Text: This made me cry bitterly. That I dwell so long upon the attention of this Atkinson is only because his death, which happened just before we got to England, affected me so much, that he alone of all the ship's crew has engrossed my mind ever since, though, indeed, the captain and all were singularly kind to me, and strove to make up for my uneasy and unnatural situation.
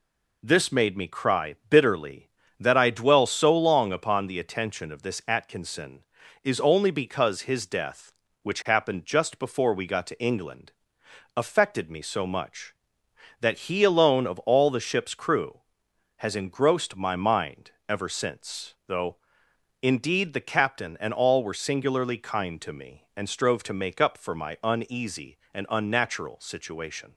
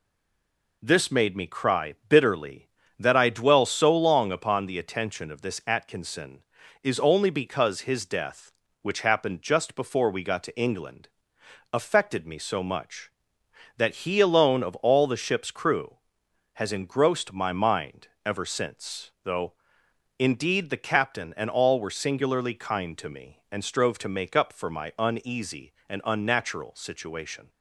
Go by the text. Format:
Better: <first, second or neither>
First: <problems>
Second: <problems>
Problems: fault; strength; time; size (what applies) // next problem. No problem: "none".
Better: first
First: pauses between "mind" and "ever"; slight; at 17.7 s; 0.18 s long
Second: stays silent before the first word; slight; until 0.8 s; 0.8 s long // pauses between "mind" and "ever"; slight; at 18.0 s; 0.18 s long